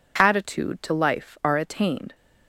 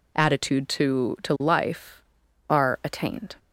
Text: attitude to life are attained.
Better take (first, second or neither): first